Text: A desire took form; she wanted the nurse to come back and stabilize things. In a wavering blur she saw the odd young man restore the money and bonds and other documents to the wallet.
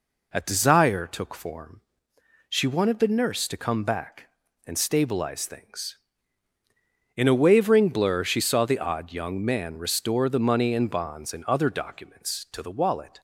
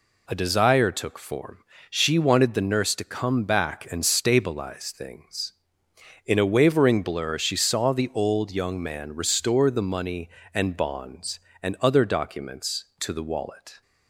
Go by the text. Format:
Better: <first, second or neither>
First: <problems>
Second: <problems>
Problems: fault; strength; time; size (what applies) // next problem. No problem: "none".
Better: first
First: none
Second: says "old" for "odd"; at 8.1 s